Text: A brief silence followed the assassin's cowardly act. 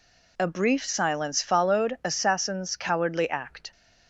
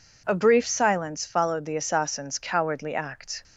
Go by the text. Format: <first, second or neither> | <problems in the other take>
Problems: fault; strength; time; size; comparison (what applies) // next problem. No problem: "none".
second | skips "the"; at 2.0 s